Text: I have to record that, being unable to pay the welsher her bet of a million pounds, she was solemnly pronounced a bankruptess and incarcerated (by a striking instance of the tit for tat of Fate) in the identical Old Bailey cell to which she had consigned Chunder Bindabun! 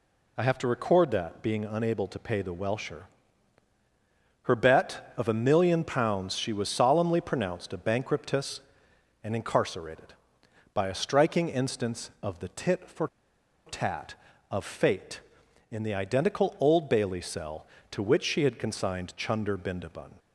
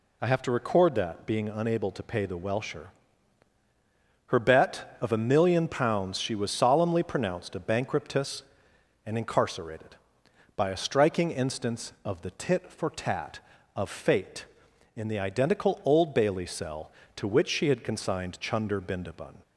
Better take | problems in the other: second | pauses between "welsher" and "her"; strong; at 3.0 s; 1.3 s long; strong in the second // pauses between "for" and "tat"; noticeable; at 13.0 s; 0.59 s long

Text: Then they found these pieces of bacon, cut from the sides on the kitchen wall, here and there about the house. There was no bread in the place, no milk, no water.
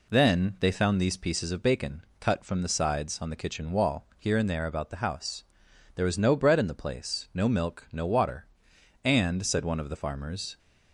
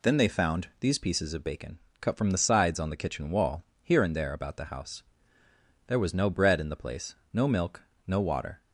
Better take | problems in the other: second | goes on to say "And said one of the farmers"; from 9.0 s on; 1.5 s long

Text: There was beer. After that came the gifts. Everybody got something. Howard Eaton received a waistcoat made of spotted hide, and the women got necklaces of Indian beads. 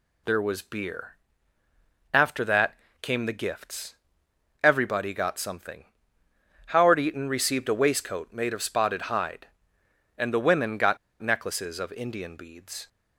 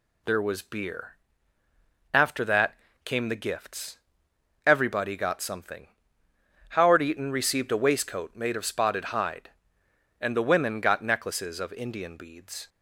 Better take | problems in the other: second | pauses between "that" and "came"; slight; at 2.7 s; 0.26 s long; slight in the second // pauses between "got" and "necklaces"; slight; at 10.9 s; 0.24 s long

